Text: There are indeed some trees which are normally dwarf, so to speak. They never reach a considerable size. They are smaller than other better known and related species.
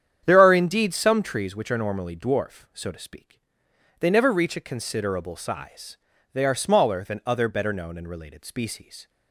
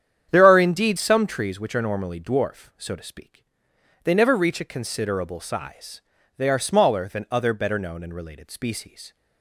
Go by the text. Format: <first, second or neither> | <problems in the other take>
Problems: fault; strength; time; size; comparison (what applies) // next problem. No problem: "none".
neither | starts louder than the rest; strong; the same in both